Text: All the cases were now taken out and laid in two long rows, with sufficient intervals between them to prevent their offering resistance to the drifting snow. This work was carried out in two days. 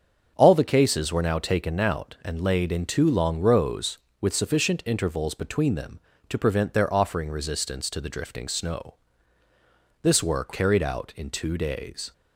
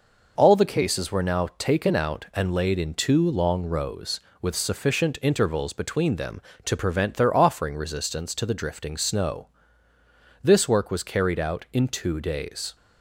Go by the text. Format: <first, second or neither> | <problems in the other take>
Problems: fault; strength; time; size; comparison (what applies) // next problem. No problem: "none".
second | starts louder than the rest; strong; until 1.3 s; 7 dB // skips "was"; at 10.5 s